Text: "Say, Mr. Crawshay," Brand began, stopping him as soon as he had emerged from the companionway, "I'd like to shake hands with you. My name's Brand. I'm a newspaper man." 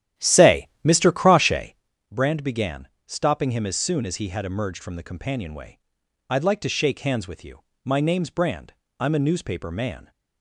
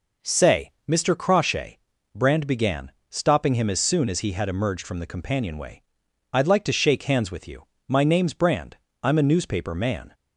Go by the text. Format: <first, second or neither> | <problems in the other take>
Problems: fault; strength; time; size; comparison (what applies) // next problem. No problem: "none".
second | starts louder than the rest; strong; until 1.9 s; 11.5 dB